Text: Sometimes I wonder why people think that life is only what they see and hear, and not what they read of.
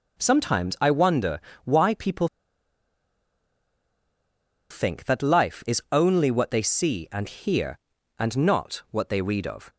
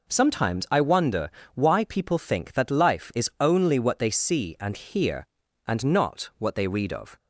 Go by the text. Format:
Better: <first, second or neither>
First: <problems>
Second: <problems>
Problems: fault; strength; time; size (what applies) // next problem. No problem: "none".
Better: second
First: pauses between "wonder" and "why"; slight; at 1.3 s; 0.26 s long // pauses between "people" and "think"; strong; at 2.2 s; 2.4 s long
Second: pauses between "wonder" and "why"; slight; at 1.2 s; 0.26 s long